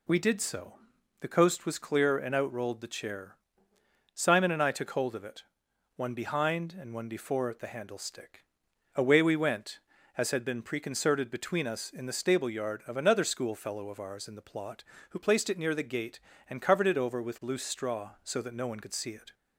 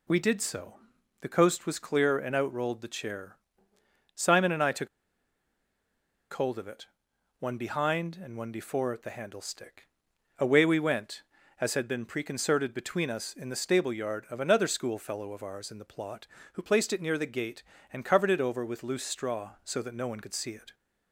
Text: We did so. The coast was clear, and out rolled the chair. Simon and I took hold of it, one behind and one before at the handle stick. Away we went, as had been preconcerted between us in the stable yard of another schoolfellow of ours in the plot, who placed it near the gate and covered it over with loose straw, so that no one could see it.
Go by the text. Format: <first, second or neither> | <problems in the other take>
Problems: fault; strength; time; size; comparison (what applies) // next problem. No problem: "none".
first | pauses between "took" and "hold"; strong; at 4.8 s; 1.4 s long